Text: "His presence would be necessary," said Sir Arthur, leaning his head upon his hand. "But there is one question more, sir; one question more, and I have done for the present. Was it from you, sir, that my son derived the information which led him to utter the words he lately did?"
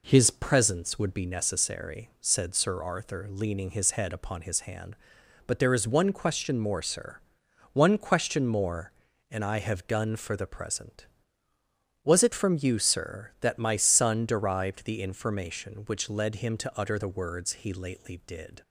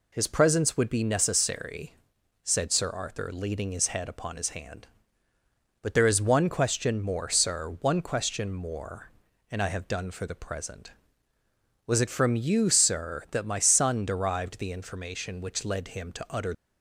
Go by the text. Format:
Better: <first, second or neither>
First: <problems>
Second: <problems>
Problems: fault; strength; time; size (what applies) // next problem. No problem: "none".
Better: first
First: none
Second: stops before "the words he lately did"; at 16.5 s